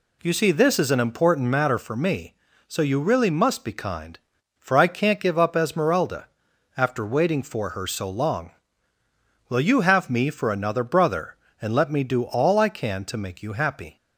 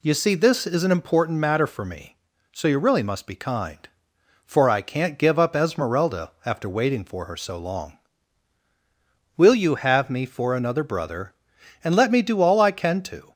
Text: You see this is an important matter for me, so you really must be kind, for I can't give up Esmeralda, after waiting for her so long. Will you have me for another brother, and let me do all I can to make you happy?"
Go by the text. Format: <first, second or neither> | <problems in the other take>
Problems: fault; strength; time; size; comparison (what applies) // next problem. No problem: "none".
first | stops before "make you happy"; at 13.3 s